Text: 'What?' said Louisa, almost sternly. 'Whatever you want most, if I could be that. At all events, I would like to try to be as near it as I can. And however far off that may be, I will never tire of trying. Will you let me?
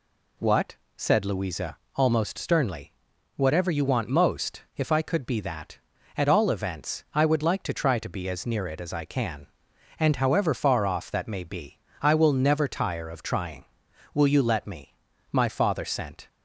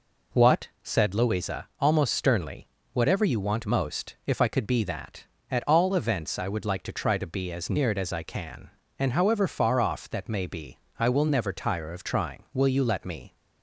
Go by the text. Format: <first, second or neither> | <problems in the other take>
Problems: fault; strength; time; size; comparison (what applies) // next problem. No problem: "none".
second | goes on to say "My father sent"; noticeable; from 15.3 s on; 0.96 s long